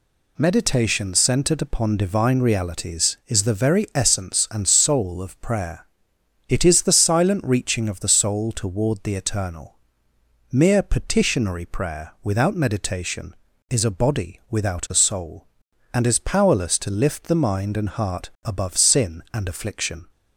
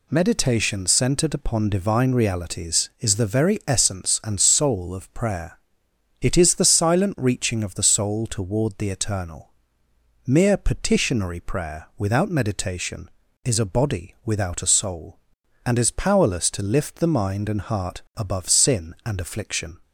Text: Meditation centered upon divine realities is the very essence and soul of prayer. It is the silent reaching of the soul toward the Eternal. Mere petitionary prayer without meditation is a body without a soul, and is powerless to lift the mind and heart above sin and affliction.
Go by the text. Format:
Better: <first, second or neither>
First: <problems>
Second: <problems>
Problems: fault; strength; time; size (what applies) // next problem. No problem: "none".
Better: neither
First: pauses between "heart" and "above"; slight; at 18.2 s; 0.16 s long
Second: pauses between "heart" and "above"; slight; at 17.9 s; 0.16 s long